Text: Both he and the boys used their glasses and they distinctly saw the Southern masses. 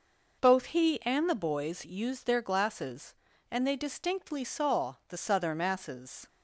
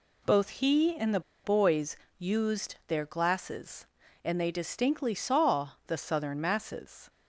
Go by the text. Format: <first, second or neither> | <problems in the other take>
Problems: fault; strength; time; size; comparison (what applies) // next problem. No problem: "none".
first | pauses between "the" and "boys"; slight; at 1.2 s; 0.23 s long // pauses between "boys" and "used"; slight; at 1.9 s; 0.22 s long // pauses between "saw" and "the"; slight; at 5.7 s; 0.16 s long